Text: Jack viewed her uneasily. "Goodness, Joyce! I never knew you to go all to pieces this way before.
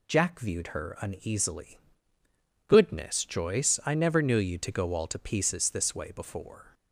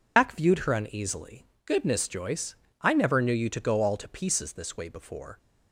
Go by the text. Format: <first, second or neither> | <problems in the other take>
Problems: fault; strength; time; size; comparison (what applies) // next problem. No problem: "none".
first | loses the start of "Jack"; at 0.1 s; 130 ms